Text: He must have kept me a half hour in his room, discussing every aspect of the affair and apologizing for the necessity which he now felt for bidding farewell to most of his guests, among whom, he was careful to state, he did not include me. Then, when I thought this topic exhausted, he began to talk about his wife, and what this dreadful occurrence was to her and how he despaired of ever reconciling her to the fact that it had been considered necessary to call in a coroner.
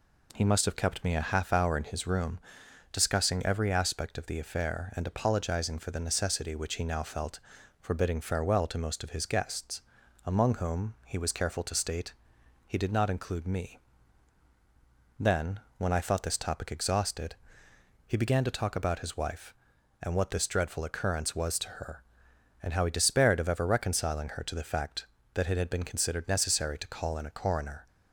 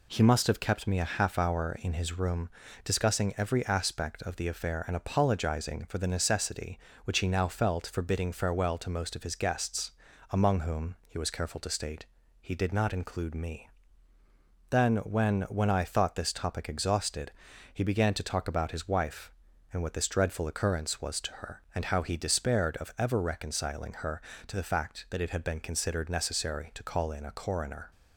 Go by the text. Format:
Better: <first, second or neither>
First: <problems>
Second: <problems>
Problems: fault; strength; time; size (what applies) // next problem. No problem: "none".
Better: first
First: none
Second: says "when" twice; at 15.4 s